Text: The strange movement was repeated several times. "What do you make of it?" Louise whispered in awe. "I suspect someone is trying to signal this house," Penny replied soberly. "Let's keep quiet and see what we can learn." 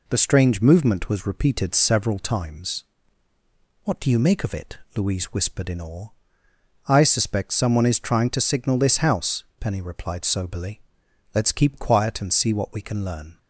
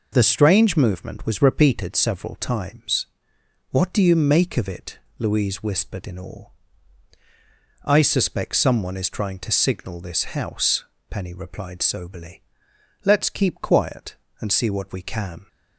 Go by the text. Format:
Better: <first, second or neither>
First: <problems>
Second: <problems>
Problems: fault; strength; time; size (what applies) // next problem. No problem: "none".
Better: first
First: none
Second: stops before "learn"; at 15.4 s